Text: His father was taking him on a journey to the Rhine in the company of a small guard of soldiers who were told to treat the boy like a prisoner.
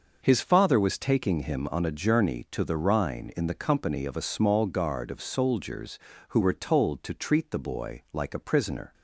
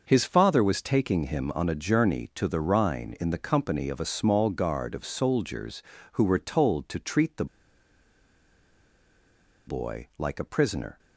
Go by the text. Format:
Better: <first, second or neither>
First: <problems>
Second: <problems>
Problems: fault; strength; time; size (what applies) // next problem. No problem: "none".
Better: first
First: none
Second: pauses between "the" and "boy"; strong; at 7.4 s; 2.2 s long